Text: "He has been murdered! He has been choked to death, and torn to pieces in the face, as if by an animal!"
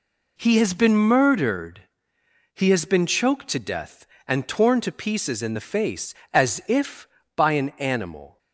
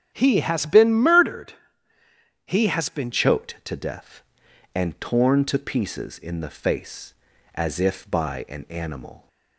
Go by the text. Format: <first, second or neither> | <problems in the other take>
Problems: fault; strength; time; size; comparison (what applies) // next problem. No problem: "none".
first | starts louder than the rest; strong; until 1.1 s; 8.5 dB // changes voice at "choked"; from 3.1 s on; 6.1 s long